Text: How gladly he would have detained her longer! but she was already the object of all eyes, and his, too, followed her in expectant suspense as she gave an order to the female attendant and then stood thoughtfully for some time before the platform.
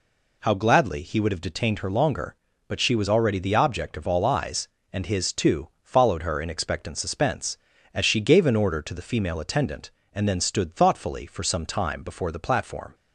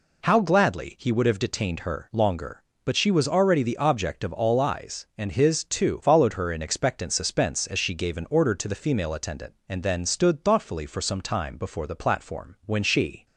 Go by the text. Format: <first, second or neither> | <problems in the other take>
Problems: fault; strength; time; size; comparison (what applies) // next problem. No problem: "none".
first | goes on to say "When she"; from 12.6 s on; 0.60 s long